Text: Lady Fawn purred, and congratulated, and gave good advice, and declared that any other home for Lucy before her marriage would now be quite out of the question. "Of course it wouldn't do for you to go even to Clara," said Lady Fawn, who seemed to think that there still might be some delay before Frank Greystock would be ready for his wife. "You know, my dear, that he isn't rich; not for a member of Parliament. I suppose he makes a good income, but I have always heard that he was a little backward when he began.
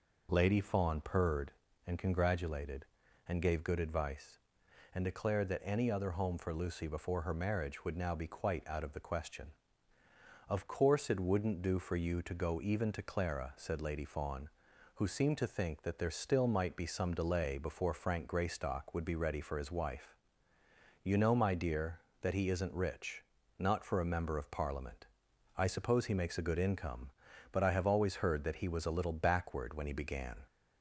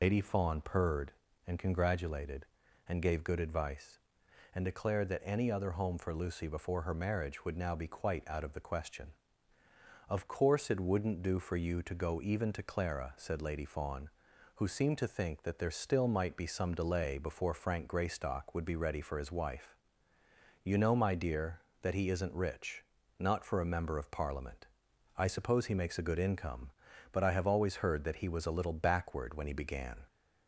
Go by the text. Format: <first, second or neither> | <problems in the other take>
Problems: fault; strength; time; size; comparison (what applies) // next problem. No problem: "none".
first | loses the start of "Lady"; at 0.0 s; 125 ms